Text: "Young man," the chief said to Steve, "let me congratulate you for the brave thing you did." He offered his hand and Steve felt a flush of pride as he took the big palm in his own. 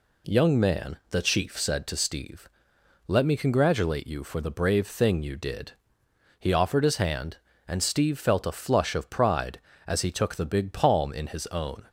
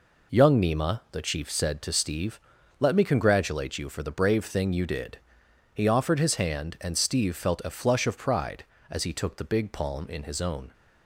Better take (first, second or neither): first